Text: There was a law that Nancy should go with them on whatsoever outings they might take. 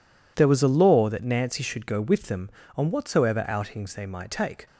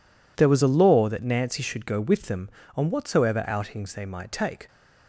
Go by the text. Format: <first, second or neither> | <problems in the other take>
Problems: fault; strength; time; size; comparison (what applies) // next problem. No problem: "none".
neither | none